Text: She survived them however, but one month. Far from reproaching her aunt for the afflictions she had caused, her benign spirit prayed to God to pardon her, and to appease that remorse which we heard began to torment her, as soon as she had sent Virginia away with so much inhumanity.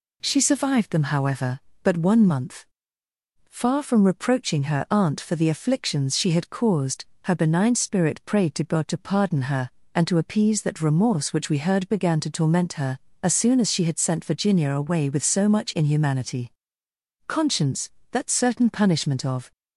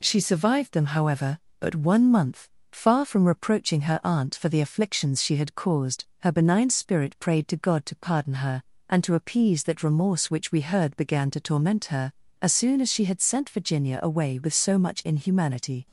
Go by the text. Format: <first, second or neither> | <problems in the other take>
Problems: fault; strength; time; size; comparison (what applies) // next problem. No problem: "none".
second | goes on to say "Conscience that certain punishment of"; strong; from 17.2 s on; 2.2 s long